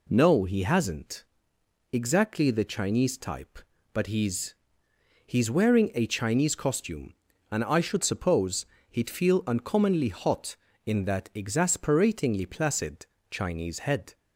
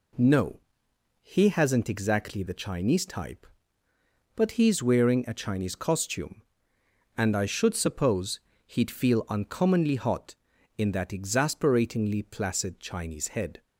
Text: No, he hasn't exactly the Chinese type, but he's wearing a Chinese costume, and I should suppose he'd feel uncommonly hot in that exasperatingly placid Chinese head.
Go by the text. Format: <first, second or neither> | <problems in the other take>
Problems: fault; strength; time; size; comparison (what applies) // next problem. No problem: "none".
second | pauses between "hasn't" and "exactly"; noticeable; at 1.2 s; 0.68 s long // says "he's" twice; at 5.2 s // pauses between "suppose" and "he'd"; slight; at 8.6 s; 0.22 s long; slight in the second // pauses between "placid" and "Chinese"; slight; at 13.0 s; 0.24 s long